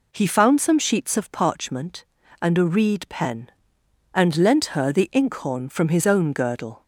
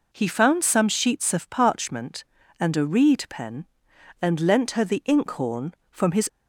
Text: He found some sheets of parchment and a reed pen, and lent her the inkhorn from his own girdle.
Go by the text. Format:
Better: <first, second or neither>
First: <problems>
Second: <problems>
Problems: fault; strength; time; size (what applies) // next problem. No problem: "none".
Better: first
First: none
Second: stops before "own girdle"; at 6.2 s